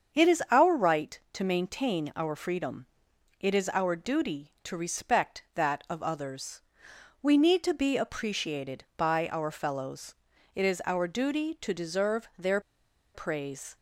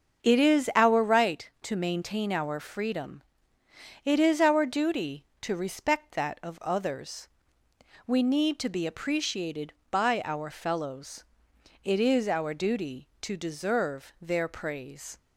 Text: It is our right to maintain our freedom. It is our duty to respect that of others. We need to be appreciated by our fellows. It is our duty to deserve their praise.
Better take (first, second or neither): second